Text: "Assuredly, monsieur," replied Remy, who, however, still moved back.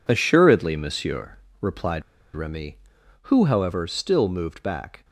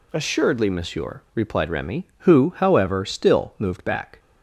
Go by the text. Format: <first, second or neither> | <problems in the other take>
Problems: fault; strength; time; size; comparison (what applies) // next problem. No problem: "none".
second | pauses between "replied" and "Remy"; slight; at 2.0 s; 0.34 s long